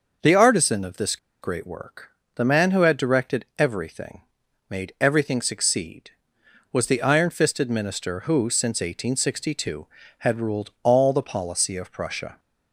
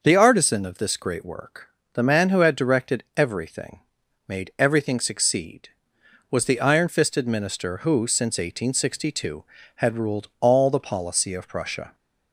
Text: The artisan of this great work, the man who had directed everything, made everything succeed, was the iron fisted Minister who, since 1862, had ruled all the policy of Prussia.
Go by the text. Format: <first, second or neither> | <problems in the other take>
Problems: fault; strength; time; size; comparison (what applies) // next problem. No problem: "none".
second | pauses between "this" and "great"; slight; at 1.1 s; 0.25 s long